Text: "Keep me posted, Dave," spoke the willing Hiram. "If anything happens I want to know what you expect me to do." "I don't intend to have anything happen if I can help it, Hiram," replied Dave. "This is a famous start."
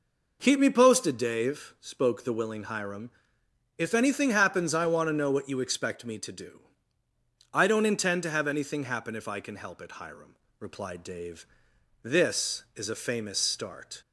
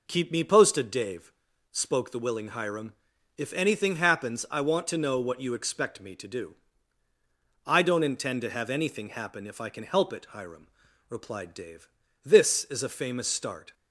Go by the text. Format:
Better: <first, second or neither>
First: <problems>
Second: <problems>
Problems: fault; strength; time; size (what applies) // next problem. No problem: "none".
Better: neither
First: none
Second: none